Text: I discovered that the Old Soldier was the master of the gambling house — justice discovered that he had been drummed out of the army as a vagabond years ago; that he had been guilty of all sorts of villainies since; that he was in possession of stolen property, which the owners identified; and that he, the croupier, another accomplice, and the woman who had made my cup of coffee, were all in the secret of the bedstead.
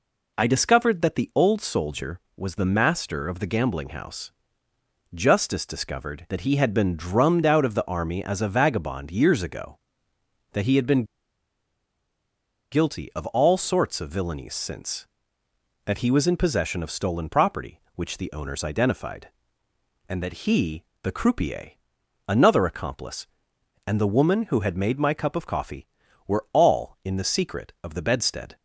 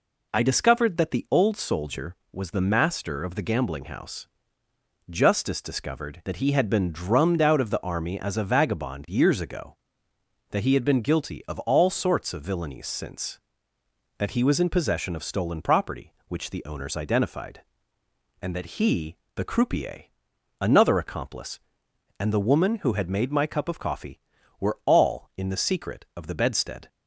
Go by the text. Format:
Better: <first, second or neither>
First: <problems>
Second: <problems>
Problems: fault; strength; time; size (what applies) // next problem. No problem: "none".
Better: second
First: pauses between "been" and "guilty"; strong; at 11.0 s; 1.6 s long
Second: none